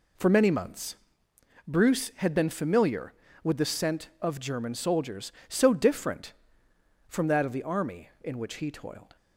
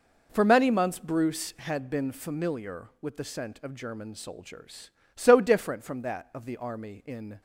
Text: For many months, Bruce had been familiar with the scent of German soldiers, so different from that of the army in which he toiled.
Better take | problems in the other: first | stops before "which he toiled"; at 7.3 s

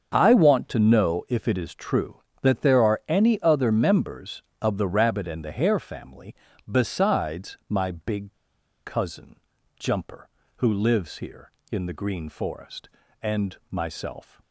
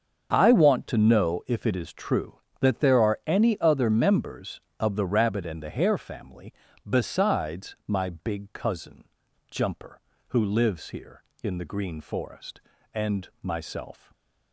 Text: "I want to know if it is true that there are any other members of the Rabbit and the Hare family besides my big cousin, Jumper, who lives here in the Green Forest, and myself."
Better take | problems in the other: second | starts louder than the rest; until 1.1 s; 6.5 dB; also in the second // pauses between "family" and "besides"; slight; at 6.3 s; 0.36 s long; slight in the second // pauses between "big" and "cousin"; noticeable; at 8.3 s; 0.50 s long

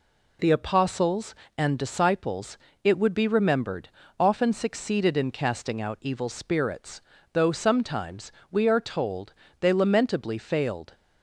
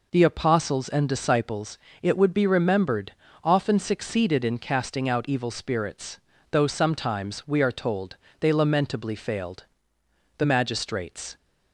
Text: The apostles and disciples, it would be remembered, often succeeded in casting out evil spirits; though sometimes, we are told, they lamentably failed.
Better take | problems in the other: first | goes on to say "The magistrates"; noticeable; from 10.3 s on; 1.0 s long

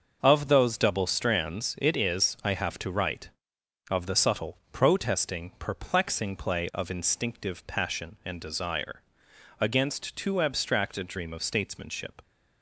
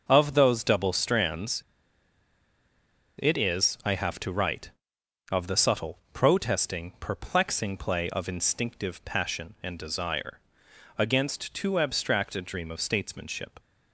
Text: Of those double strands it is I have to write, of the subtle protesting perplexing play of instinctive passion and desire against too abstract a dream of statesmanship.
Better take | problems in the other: first | pauses between "strands" and "it"; strong; at 1.6 s; 1.5 s long // pauses between "subtle" and "protesting"; slight; at 5.9 s; 0.16 s long; slight in the first // pauses between "desire" and "against"; noticeable; at 10.3 s; 0.60 s long; noticeable in the first

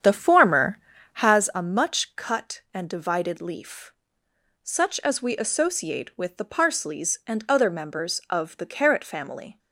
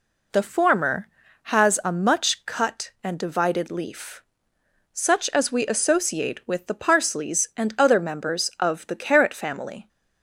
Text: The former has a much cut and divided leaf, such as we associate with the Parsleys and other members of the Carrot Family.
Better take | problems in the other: second | starts louder than the rest; strong; until 1.5 s; 8.5 dB

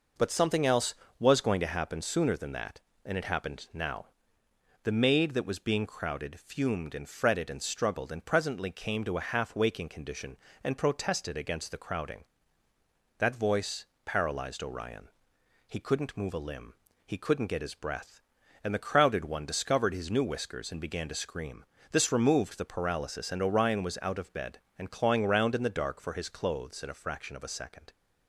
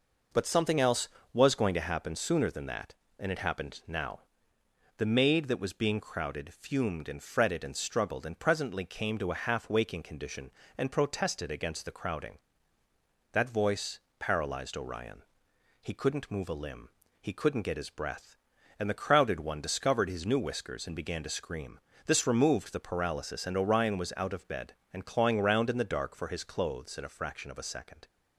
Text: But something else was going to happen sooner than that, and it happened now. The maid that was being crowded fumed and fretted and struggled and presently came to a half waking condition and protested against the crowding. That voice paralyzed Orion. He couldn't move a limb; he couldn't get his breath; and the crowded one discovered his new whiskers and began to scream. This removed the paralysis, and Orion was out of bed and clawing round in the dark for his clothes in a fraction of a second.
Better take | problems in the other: neither | pauses between "voice" and "paralyzed"; slight; the same in both

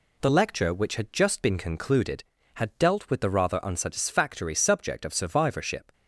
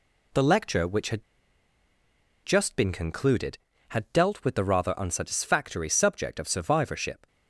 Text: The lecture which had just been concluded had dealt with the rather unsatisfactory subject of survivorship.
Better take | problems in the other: first | pauses between "had" and "just"; at 1.2 s; 1.2 s long

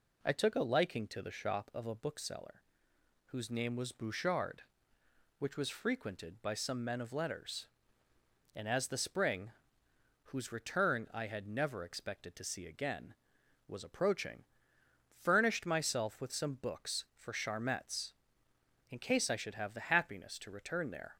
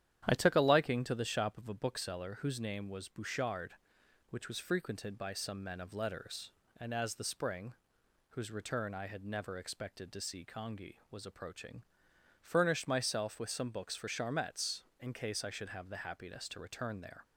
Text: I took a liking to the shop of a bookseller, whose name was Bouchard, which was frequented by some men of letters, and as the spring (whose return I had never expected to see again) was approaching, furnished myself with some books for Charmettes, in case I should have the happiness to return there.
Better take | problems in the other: first | starts louder than the rest; strong; until 1.2 s; 10.5 dB // says "congi" for "again"; at 10.4 s

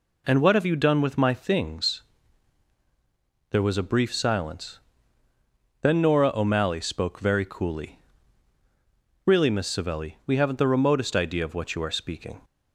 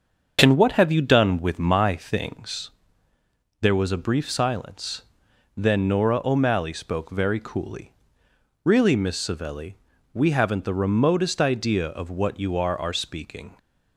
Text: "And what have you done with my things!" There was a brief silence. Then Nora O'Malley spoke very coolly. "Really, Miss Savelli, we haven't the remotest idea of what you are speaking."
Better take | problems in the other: first | starts louder than the rest; until 1.4 s; 6.5 dB // says "are" twice; at 12.7 s

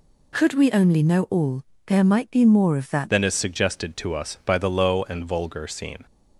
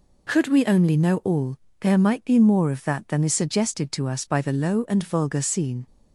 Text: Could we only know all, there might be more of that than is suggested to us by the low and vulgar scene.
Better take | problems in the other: second | changes voice at "than"; from 3.0 s on; 3.0 s long

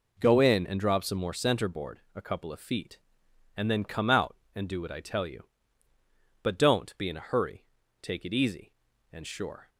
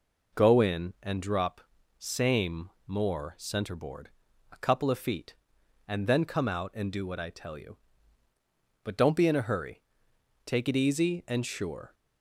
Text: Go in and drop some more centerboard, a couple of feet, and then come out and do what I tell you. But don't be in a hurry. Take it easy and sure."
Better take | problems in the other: first | says "same" for "some"; at 1.9 s

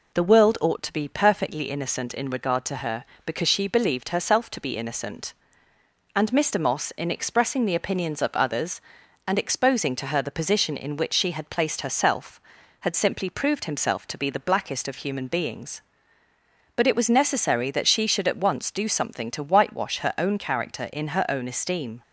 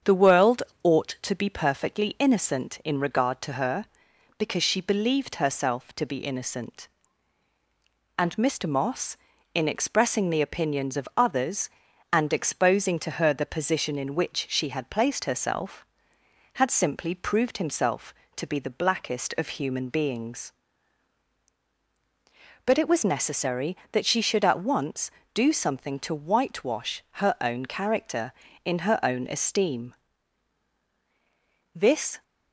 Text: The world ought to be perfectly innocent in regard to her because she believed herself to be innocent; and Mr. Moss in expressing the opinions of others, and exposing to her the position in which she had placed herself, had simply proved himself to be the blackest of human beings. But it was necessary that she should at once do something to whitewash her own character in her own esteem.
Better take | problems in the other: first | starts louder than the rest; strong; until 1.3 s; 7.5 dB // pauses between "world" and "ought"; slight; at 0.6 s; 0.20 s long // pauses between "whitewash" and "her"; slight; at 27.0 s; 0.18 s long // goes on to say "This"; slight; from 31.7 s on; 0.48 s long

